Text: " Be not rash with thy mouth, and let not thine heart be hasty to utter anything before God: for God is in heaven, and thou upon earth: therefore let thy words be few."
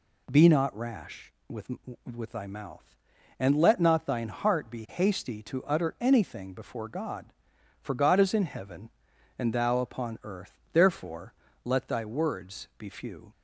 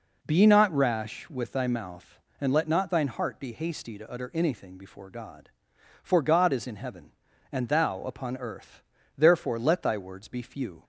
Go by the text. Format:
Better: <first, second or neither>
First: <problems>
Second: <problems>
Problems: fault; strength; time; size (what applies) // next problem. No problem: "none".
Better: second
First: says "with" twice; at 2.0 s // pauses between "therefore" and "let"; slight; at 11.3 s; 0.30 s long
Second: none